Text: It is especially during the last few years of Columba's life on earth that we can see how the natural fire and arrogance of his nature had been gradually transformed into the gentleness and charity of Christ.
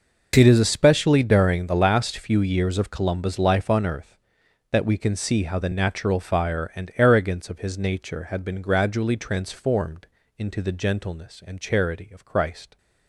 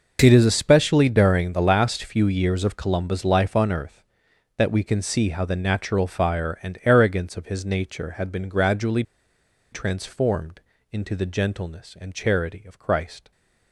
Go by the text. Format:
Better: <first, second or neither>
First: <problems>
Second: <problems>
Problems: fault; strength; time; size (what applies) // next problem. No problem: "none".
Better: first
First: pauses between "transformed" and "into"; slight; at 10.0 s; 0.32 s long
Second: pauses between "gradually" and "transformed"; noticeable; at 9.0 s; 0.69 s long // pauses between "transformed" and "into"; slight; at 10.6 s; 0.32 s long